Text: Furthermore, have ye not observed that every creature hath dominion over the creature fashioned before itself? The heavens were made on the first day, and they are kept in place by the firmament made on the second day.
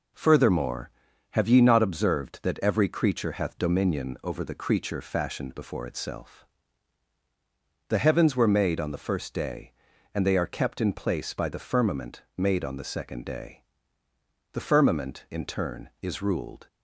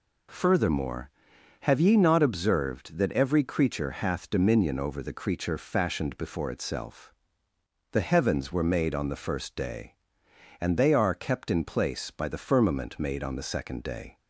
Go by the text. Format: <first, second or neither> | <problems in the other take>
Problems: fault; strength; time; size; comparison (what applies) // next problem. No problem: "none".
second | goes on to say "The firmament in turn is ruled"; strong; from 14.5 s on; 2.1 s long